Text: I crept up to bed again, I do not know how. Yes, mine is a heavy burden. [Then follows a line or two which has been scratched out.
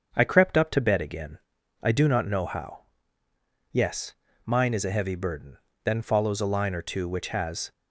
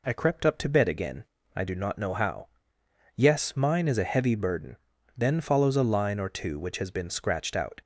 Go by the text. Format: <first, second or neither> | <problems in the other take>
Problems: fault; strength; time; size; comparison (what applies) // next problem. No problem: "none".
second | starts louder than the rest; until 1.1 s; 7 dB // stops before "been scratched out"; at 7.7 s